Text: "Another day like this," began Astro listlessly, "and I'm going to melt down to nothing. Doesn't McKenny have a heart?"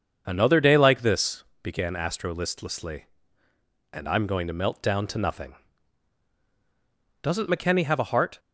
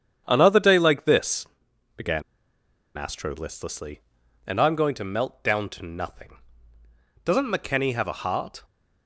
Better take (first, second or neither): first